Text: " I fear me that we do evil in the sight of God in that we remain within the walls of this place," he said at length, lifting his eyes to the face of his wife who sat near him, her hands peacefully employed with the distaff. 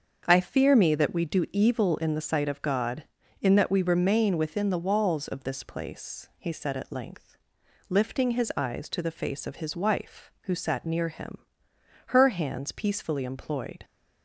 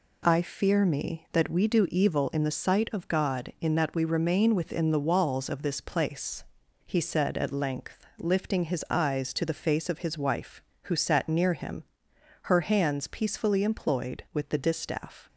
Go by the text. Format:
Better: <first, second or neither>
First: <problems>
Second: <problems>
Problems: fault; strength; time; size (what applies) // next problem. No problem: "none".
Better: second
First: starts louder than the rest; until 1.2 s; 7 dB // stops before "with the distaff"; at 13.8 s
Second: none